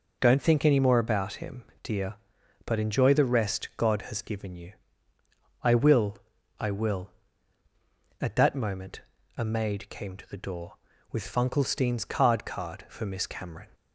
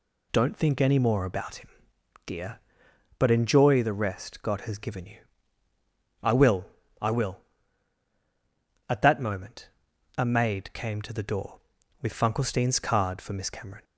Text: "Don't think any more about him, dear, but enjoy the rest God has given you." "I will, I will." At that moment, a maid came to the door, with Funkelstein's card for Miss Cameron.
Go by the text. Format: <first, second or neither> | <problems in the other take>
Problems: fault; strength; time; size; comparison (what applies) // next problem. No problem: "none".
second | says "card" twice; at 12.4 s